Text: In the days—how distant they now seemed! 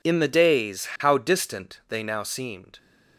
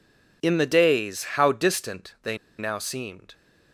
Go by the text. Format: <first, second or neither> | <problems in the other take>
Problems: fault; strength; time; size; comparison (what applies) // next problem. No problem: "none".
first | pauses between "they" and "now"; slight; at 2.3 s; 0.21 s long